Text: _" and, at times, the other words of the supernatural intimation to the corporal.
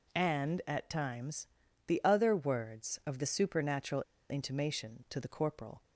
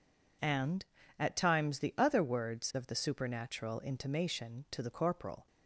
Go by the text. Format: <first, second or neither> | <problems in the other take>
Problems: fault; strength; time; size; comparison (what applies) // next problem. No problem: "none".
second | pauses between "supernatural" and "intimation"; slight; at 4.0 s; 0.27 s long